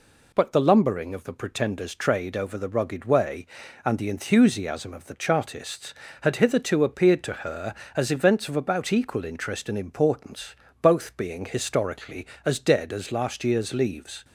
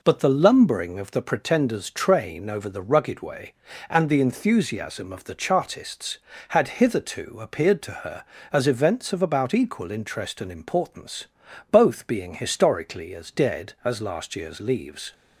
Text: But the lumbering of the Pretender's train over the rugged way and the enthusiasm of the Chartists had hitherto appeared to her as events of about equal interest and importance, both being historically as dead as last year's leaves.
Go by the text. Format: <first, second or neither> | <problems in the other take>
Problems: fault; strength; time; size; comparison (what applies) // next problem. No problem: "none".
second | says "trade" for "train"; at 1.9 s